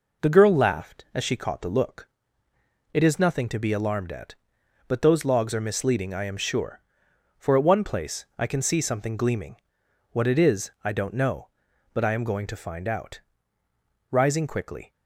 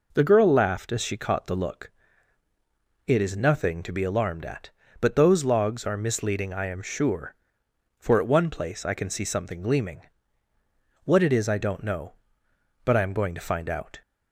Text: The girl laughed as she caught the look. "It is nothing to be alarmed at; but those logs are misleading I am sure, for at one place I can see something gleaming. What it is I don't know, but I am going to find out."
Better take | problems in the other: second | goes on to say "Rising quickly"; noticeable; from 14.1 s on; 0.80 s long

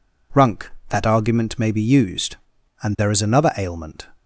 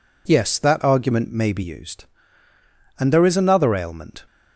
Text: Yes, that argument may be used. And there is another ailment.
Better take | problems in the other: second | says "Runk" for "Yes"; at 0.3 s

